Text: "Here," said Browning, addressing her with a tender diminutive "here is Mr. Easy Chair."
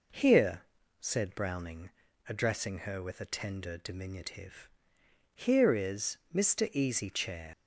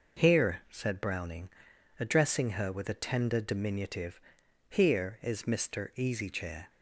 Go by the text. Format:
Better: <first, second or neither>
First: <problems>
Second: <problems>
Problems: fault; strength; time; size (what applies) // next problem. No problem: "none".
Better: second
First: pauses between "diminutive" and "here"; noticeable; at 4.6 s; 0.68 s long // leaves "Chair" unfinished; at 7.5 s; 85 ms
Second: pauses between "diminutive" and "here"; noticeable; at 4.1 s; 0.48 s long